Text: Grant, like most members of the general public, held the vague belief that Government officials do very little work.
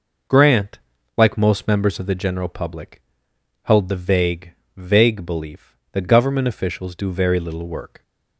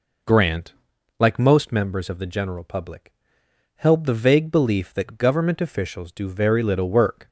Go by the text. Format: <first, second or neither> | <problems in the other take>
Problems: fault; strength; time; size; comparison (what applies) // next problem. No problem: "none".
second | says "vague" twice; at 4.7 s